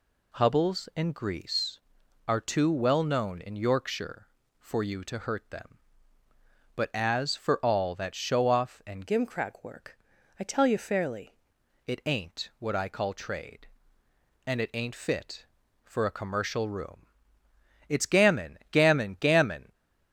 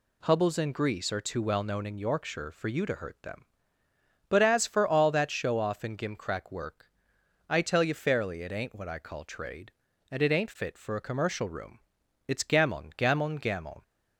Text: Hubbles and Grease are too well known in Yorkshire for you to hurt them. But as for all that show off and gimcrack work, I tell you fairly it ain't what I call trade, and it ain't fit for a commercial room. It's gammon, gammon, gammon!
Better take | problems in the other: second | changes voice from "gimcrack" to "fairly"; from 9.0 to 11.3 s; 2.3 s long

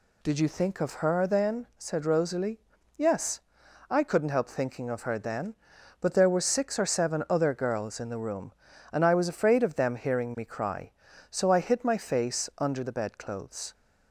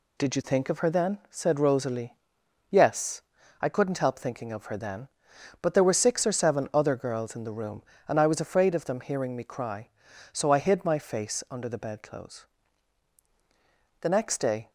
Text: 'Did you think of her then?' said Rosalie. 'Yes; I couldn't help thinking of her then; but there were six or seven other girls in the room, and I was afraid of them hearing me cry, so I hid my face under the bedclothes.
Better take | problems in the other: first | goes on to say "The next day"; noticeable; from 13.9 s on; 0.70 s long

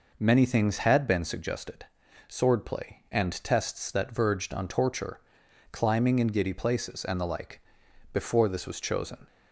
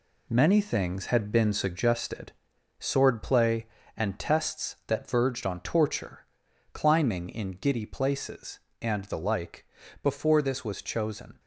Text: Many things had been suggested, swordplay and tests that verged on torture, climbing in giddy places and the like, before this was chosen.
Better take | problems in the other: first | gets quieter; strong; throughout; 7.5 dB

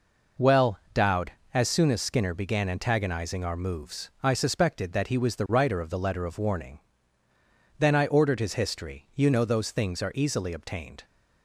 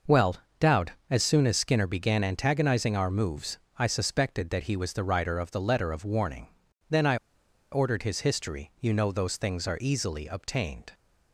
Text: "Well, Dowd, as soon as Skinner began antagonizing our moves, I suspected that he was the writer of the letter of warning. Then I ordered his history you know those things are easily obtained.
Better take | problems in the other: first | pauses between "I" and "ordered"; noticeable; at 7.1 s; 0.55 s long

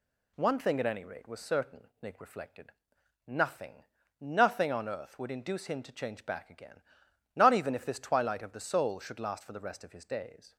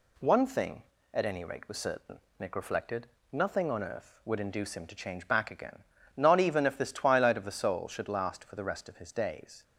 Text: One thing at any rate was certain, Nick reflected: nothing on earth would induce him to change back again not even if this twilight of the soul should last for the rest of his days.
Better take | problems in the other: second | says "nothing" twice; at 4.2 s // pauses between "again" and "not"; noticeable; at 6.7 s; 0.56 s long; slight in the second

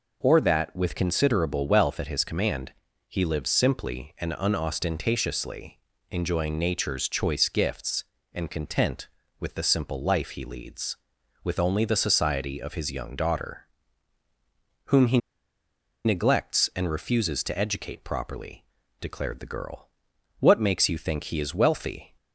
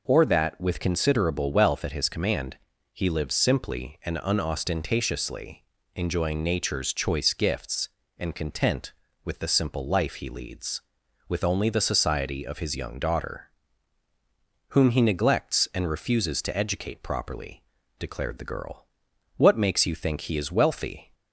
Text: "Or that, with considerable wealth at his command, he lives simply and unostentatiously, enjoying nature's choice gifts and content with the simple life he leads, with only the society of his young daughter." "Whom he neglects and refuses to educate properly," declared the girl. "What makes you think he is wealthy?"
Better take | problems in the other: second | pauses between "he" and "neglects"; noticeable; at 15.1 s; 0.87 s long

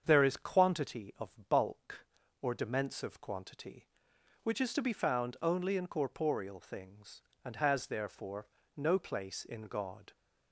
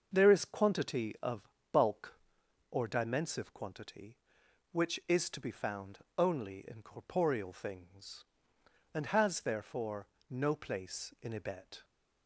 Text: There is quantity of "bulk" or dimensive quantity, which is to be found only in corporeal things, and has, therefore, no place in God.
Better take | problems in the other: first | starts louder than the rest; until 1.1 s; 6 dB; strong in the first // pauses between "of" and "bulk"; slight; at 1.4 s; 0.24 s long // pauses between "found" and "only"; slight; at 6.0 s; 0.18 s long // says "Ibet" for "God"; at 11.3 s

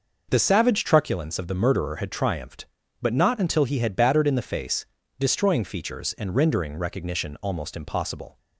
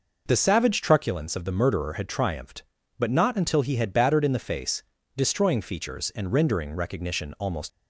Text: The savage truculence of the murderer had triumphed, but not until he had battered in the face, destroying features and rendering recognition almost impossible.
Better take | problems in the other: first | stops before "impossible"; at 7.6 s

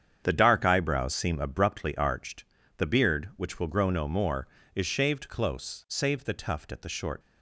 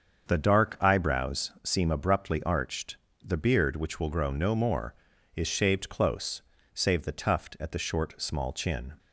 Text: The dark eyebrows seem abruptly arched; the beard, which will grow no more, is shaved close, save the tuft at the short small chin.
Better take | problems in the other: second | starts louder than the rest; strong; until 1.2 s; 8 dB; also in the second // stops before "small chin"; at 7.2 s

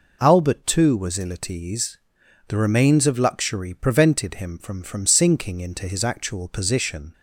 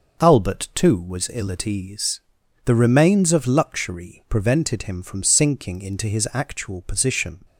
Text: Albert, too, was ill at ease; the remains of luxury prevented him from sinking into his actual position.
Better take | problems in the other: second | says "from" twice; at 4.8 s

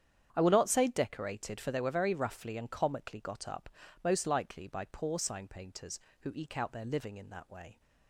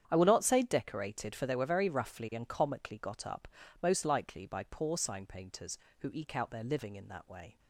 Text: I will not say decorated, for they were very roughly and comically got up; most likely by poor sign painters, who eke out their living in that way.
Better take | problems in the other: neither | starts louder than the rest; strong; the same in both

